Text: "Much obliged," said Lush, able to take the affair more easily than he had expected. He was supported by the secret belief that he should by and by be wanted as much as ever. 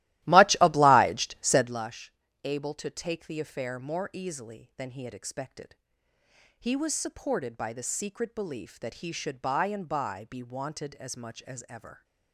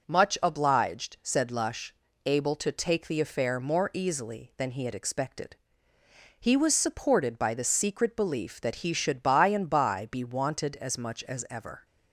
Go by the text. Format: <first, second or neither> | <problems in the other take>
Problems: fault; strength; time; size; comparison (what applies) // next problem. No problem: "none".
second | starts louder than the rest; strong; until 1.8 s; 16 dB